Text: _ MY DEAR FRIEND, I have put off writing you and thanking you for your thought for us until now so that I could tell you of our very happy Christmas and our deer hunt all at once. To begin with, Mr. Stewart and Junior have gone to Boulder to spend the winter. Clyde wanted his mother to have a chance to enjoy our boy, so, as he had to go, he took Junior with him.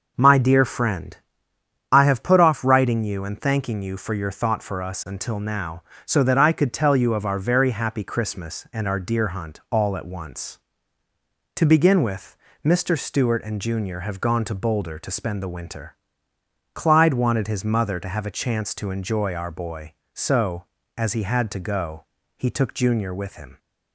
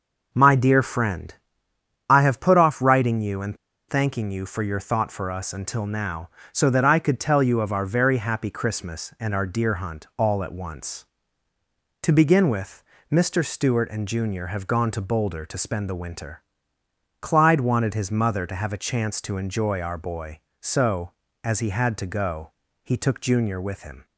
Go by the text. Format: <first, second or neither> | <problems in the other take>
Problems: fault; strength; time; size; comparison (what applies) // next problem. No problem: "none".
first | pauses between "and" and "thanking"; slight; at 3.5 s; 0.32 s long